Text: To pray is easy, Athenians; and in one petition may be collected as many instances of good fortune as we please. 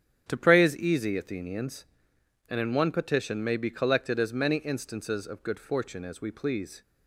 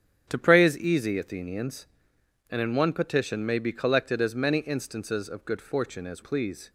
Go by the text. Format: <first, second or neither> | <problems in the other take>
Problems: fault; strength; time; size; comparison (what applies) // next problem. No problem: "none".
first | starts louder than the rest; strong; until 1.3 s; 9 dB; strong in the first // skips "we"; at 6.2 s